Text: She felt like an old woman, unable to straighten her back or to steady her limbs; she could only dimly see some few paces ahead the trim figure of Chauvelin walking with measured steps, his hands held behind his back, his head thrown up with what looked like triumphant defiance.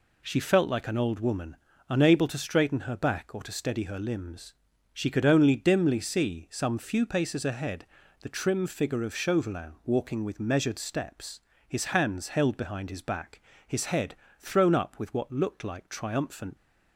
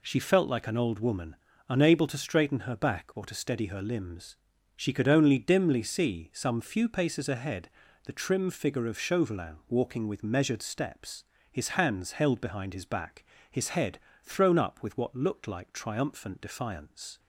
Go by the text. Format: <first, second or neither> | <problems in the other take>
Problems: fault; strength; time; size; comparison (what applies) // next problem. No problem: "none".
second | pauses between "ahead" and "the"; slight; at 7.8 s; 0.36 s long; slight in the second // pauses between "head" and "thrown"; slight; at 14.1 s; 0.24 s long; slight in the second // stops before "defiance"; at 16.5 s